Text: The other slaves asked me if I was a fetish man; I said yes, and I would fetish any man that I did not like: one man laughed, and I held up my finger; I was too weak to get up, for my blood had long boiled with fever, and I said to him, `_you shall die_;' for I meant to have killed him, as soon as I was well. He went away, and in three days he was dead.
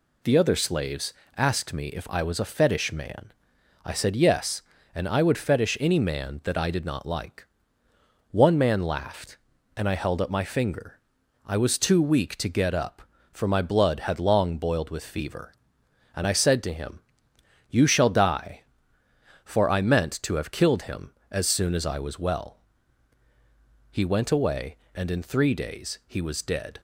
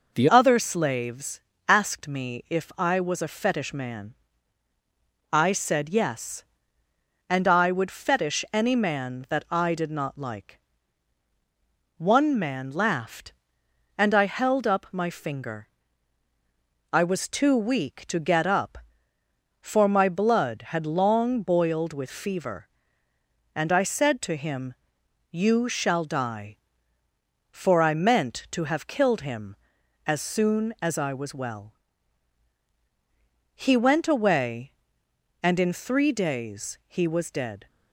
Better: first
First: pauses between "slaves" and "asked"; slight; at 1.1 s; 0.24 s long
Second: changes voice at "other"; from 0.2 s on; 37.4 s long // pauses between "slaves" and "asked"; slight; at 1.4 s; 0.28 s long

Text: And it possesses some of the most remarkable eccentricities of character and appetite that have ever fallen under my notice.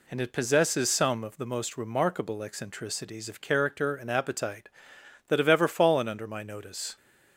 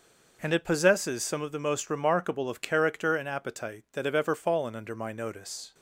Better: first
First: none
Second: skips "eccentricities"; at 2.4 s

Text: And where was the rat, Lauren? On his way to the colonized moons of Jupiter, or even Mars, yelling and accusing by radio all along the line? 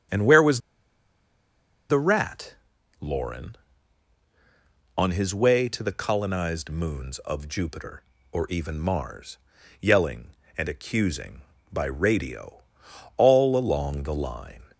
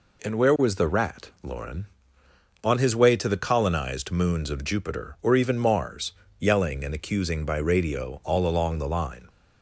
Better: second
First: starts louder than the rest; strong; until 2.4 s; 9 dB // pauses between "was" and "the"; strong; at 0.5 s; 1.3 s long // pauses between "radio" and "all"; noticeable; at 12.6 s; 0.54 s long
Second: none

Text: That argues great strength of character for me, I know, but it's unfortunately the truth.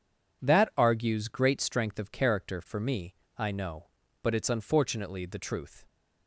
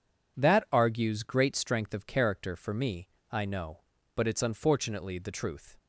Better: neither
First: none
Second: none

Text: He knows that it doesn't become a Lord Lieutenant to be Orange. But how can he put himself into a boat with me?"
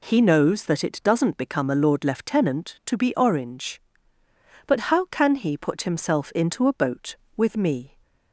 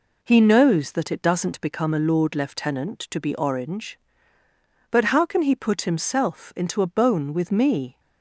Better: first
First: none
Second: says "bone" for "boat"; at 6.8 s

